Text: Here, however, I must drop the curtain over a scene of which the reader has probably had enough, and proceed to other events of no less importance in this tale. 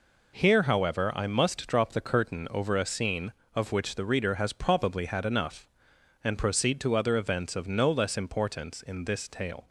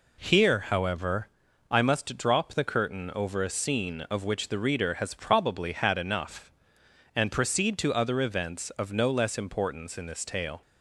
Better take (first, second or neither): neither